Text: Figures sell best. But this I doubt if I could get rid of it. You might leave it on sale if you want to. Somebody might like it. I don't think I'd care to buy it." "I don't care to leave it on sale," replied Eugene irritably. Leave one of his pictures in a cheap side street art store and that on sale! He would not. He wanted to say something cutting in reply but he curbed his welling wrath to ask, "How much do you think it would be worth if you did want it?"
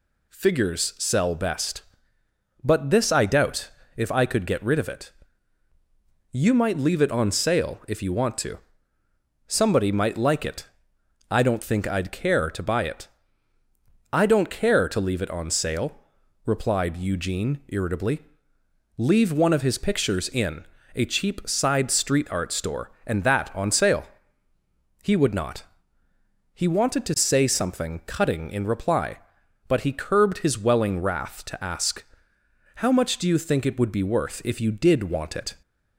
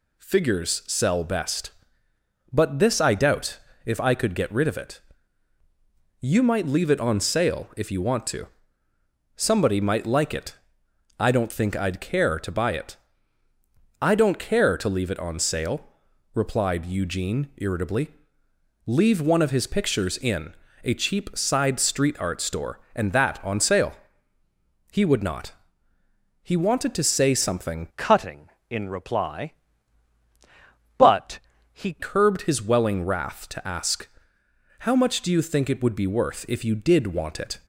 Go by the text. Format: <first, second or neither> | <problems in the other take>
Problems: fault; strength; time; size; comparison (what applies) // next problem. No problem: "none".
first | pauses between "doubt" and "if"; slight; at 3.6 s; 0.26 s long; slight in the first // pauses between "in" and "a"; slight; at 20.5 s; 0.30 s long; slight in the first // changes voice from "cutting" to "he"; from 27.9 to 31.9 s; 4.0 s long // pauses between "but" and "he"; slight; at 31.3 s; 0.34 s long